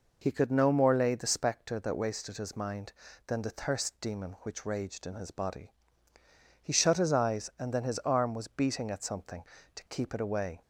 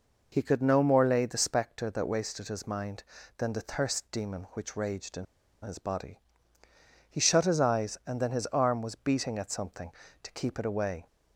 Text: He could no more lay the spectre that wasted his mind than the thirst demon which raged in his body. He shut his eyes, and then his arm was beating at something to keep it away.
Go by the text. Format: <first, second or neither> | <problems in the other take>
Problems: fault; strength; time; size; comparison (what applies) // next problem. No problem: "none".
first | pauses between "in" and "his"; at 5.2 s; 0.37 s long